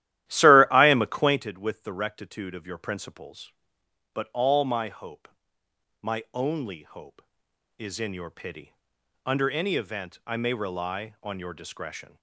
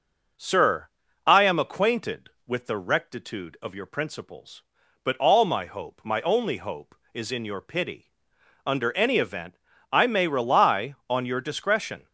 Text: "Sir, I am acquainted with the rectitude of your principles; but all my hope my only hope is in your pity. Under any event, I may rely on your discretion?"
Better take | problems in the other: second | starts louder than the rest; strong; until 1.5 s; 13.5 dB // pauses between "hope" and "my"; noticeable; at 5.2 s; 0.74 s long

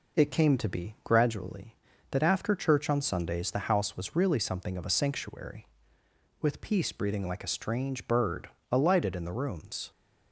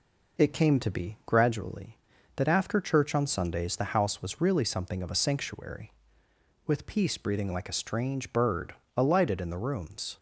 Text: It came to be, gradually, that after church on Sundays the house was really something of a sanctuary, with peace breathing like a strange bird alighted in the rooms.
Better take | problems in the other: neither | pauses between "bird" and "alighted"; slight; the same in both

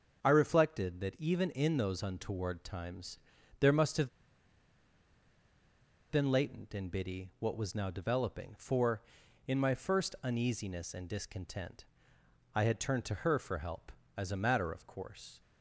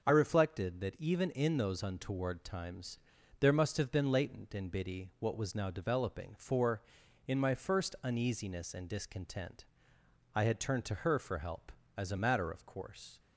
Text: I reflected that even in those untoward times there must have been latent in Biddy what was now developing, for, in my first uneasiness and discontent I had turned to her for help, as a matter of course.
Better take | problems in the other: second | starts louder than the rest; until 1.2 s; 6.5 dB; also in the second // pauses between "times" and "there"; at 3.1 s; 0.44 s long; also in the second // pauses between "have" and "been"; strong; at 4.0 s; 2.0 s long // pauses between "discontent" and "I"; noticeable; at 11.8 s; 0.68 s long; noticeable in the second

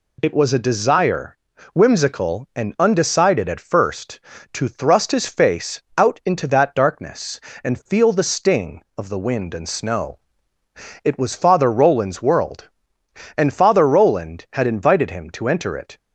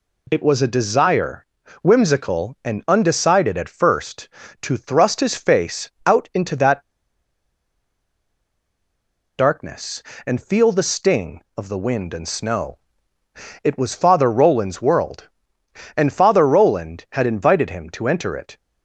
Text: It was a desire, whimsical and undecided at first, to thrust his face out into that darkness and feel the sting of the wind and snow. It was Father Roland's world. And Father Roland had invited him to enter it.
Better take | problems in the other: first | pauses between "face" and "out"; slight; at 5.8 s; 0.16 s long; slight in the first // pauses between "that" and "darkness"; strong; at 6.8 s; 2.5 s long

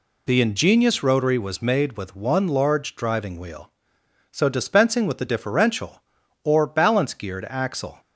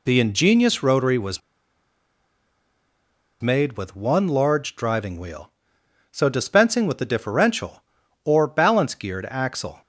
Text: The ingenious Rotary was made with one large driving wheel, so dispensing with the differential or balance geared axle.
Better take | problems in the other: first | pauses between "was" and "made"; strong; at 1.4 s; 2.0 s long

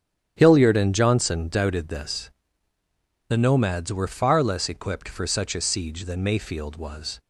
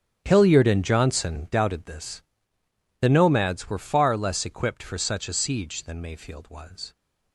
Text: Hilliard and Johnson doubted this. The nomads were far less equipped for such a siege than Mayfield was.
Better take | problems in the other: first | gets quieter; strong; throughout; 15.5 dB // starts louder than the rest; strong; until 1.2 s; 9 dB; strong in the first

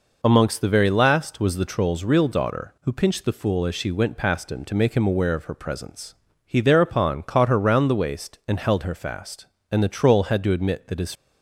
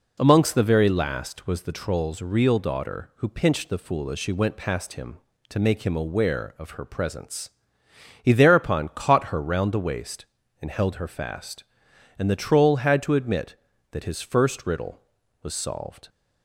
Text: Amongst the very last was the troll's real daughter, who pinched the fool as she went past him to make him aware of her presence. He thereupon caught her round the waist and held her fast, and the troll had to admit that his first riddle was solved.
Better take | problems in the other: second | stops before "first riddle was solved"; at 11.1 s

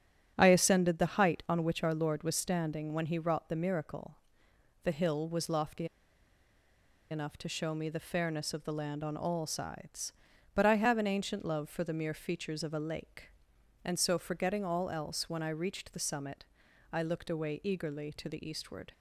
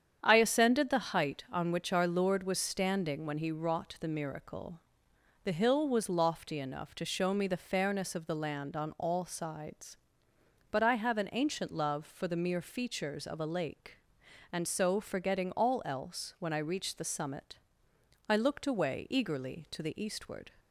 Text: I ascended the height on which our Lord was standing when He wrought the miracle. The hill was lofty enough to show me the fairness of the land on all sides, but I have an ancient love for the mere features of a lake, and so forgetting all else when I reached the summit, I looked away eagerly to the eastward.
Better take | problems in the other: second | starts louder than the rest; strong; until 1.3 s; 8.5 dB; strong in the second // pauses between "lofty" and "enough"; strong; at 5.8 s; 1.2 s long

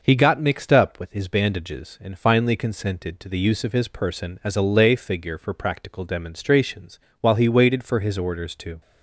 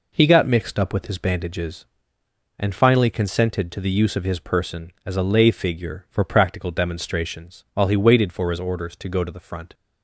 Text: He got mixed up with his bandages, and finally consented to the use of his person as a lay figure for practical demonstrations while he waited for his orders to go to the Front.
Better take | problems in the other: second | pauses between "demonstrations" and "while"; slight; at 6.9 s; 0.22 s long // stops before "go to the Front"; at 8.8 s

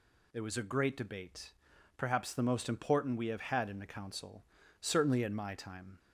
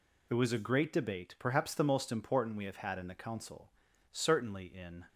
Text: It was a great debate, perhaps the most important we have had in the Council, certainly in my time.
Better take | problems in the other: first | stops before "my time"; at 5.0 s

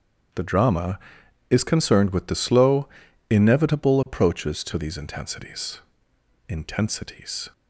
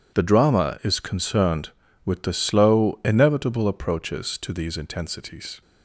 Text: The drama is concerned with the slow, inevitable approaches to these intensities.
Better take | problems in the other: second | starts louder than the rest; strong; until 1.8 s; 8.5 dB; strong in the second // says "intensities" twice; at 6.4 s

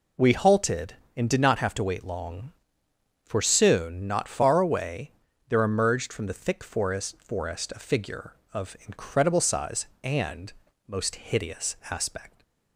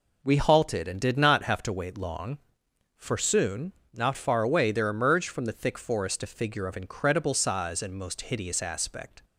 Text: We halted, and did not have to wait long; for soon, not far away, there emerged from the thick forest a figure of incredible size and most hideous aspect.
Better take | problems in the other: second | says "forest" twice; at 7.2 s // pauses between "and" and "most"; at 10.5 s; 0.38 s long

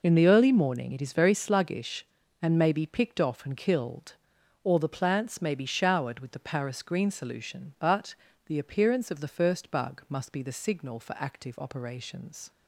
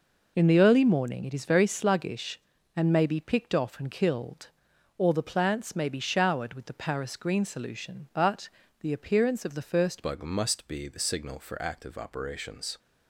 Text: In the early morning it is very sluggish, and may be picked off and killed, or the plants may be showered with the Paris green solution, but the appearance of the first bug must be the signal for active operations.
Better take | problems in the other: first | pauses between "but" and "the"; slight; at 8.4 s; 0.30 s long; slight in the first // changes voice at "bug"; from 10.0 s on; 2.7 s long

